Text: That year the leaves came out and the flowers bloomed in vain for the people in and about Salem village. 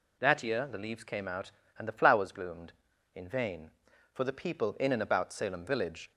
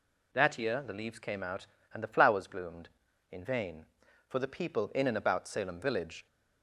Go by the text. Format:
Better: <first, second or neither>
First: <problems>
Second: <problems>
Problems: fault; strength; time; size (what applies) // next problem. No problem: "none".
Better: neither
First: none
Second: none